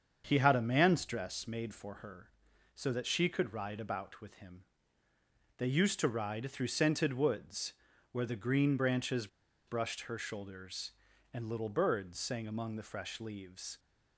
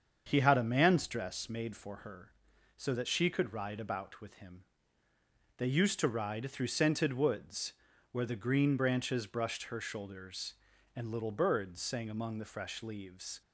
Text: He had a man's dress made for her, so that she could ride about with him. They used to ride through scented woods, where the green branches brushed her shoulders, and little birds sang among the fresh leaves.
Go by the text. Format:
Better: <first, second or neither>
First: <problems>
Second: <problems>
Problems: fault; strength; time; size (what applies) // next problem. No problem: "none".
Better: second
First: starts louder than the rest; until 1.2 s; 7 dB // pauses between "branches" and "brushed"; at 9.2 s; 0.39 s long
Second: starts louder than the rest; until 1.2 s; 7 dB